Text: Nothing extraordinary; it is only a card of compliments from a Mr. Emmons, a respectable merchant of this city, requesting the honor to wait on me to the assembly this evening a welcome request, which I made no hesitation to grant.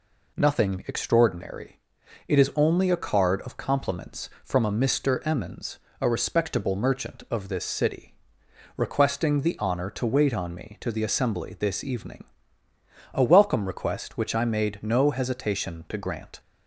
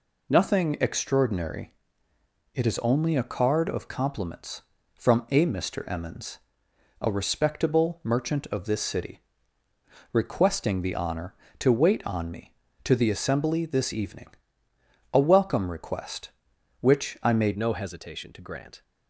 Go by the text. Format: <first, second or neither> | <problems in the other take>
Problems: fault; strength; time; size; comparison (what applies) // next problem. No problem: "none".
first | pauses between "evening" and "a"; noticeable; at 14.2 s; 0.84 s long; noticeable in the first // changes voice at "no"; from 17.5 s on; 1.3 s long